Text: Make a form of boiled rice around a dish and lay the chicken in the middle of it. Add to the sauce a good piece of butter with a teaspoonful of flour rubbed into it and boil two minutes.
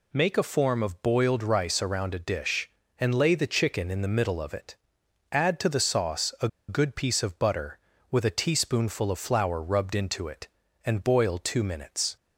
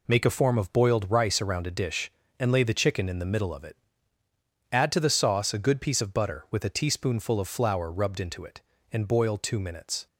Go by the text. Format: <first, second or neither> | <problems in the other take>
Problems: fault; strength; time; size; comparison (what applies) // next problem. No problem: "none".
second | pauses between "a" and "good"; slight; at 6.4 s; 0.21 s long